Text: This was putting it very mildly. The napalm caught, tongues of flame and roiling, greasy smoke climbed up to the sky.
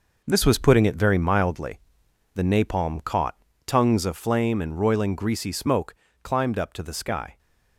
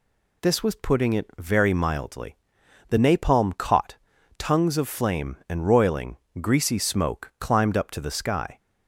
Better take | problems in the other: second | gets quieter; strong; throughout; 7.5 dB // pauses between "smoke" and "climbed"; slight; at 5.9 s; 0.26 s long

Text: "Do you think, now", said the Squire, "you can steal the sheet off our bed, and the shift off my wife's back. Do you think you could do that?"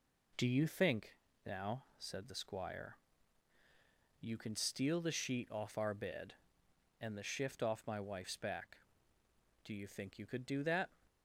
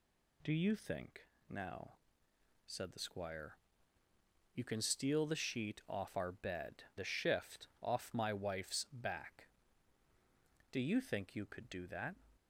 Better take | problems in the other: first | skips "and"; at 6.9 s

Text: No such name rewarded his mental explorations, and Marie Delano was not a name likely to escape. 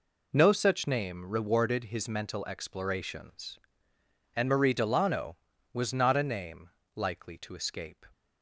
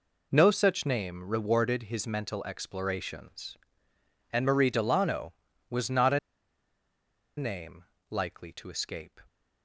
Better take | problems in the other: first | pauses between "a" and "name"; at 6.1 s; 1.1 s long // pauses between "name" and "likely"; slight; at 7.8 s; 0.24 s long; slight in the first

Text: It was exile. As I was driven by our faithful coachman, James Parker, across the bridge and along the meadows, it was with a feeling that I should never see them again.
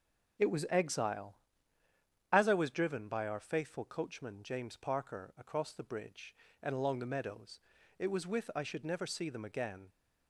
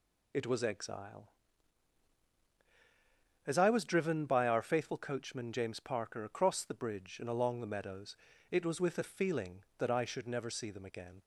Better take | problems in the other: second | starts louder than the rest; strong; until 2.4 s; 9 dB // skips "a feeling that"; at 8.5 s

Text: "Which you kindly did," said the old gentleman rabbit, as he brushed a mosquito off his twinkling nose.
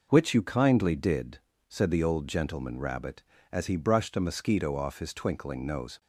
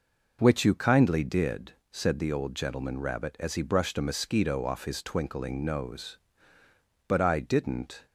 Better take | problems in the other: first | goes on to say "But I didn't"; noticeable; from 7.0 s on; 0.98 s long

